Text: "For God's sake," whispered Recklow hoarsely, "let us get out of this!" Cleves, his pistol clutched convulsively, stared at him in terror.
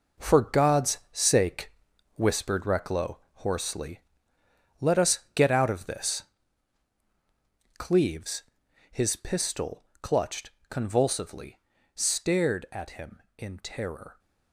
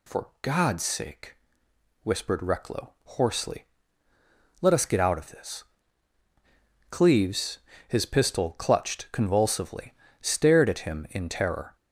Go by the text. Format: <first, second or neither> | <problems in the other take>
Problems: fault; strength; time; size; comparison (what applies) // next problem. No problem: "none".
second | gets quieter; strong; throughout; 10 dB // pauses between "Recklow" and "hoarsely"; slight; at 3.1 s; 0.16 s long // pauses between "pistol" and "clutched"; slight; at 9.8 s; 0.16 s long // pauses between "clutched" and "convulsively"; slight; at 10.5 s; 0.18 s long